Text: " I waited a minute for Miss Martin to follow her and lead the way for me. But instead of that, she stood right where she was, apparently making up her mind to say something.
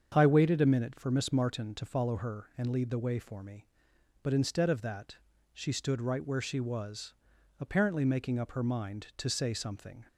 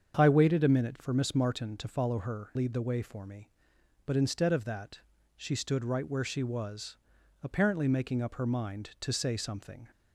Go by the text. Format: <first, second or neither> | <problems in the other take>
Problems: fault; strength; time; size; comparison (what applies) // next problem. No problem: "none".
first | starts louder than the rest; strong; until 1.1 s; 7 dB; strong in the first // skips "and"; at 2.5 s